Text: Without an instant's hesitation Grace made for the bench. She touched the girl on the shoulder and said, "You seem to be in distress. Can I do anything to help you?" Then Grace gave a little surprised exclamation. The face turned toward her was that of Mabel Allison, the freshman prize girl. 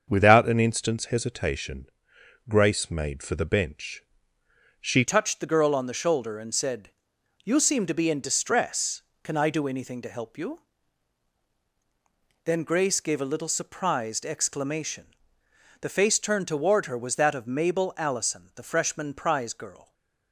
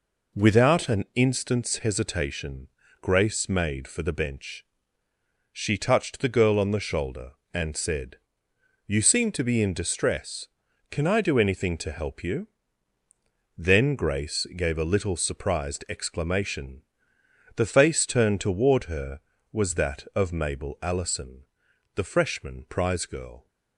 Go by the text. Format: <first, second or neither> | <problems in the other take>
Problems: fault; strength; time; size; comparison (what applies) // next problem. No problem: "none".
second | starts louder than the rest; until 1.0 s; 6.5 dB // pauses between "hesitation" and "Grace"; noticeable; at 1.8 s; 0.62 s long; slight in the second // changes voice at "touched"; from 5.0 s on; 14.9 s long